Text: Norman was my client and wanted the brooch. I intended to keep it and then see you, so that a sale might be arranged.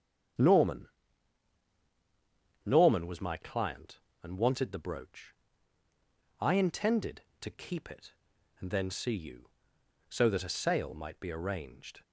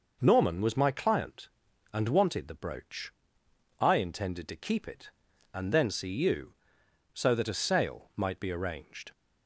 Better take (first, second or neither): second